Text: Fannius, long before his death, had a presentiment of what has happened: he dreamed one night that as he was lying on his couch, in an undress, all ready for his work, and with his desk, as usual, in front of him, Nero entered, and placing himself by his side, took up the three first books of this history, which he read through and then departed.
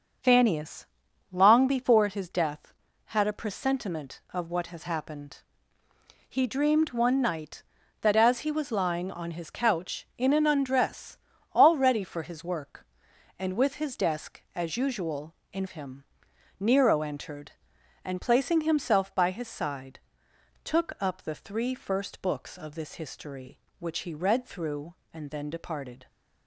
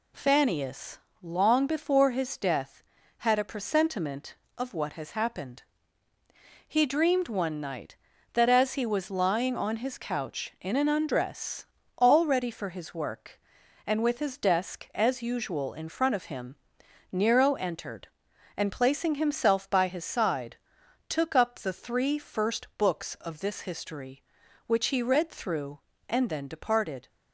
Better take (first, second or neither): second